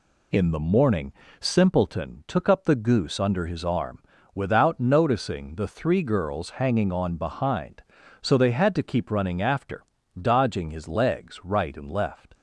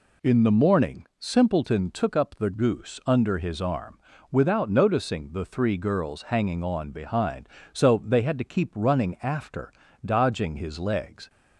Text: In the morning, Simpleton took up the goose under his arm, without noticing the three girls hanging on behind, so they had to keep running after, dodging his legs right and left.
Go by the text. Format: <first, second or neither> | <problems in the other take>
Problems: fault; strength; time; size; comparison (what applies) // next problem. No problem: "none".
first | stops before "right and left"; at 11.2 s